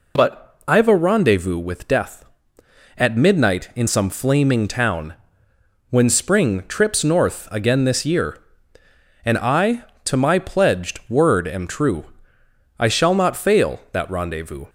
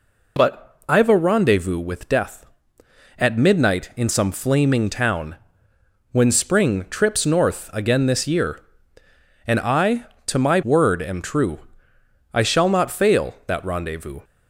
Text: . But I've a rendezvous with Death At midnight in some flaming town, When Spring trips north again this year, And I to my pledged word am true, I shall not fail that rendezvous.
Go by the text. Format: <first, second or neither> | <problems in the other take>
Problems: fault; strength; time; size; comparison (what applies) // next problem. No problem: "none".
first | skips "pledged"; at 10.6 s